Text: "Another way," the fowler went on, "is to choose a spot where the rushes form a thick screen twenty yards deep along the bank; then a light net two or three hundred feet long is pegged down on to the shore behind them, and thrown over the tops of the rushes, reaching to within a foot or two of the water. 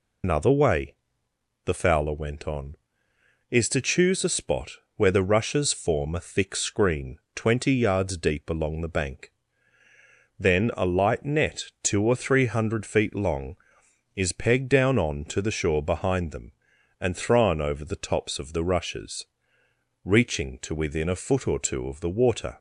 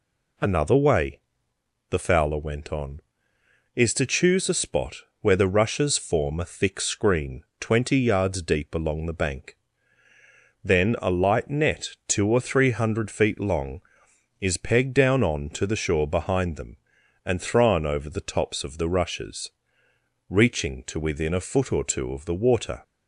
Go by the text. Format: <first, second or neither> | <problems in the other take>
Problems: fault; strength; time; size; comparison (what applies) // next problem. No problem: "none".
second | loses the start of "Another"; at 0.2 s; 100 ms // pauses between "spot" and "where"; slight; at 4.7 s; 0.24 s long; slight in the second // pauses between "screen" and "twenty"; slight; at 7.1 s; 0.16 s long; slight in the second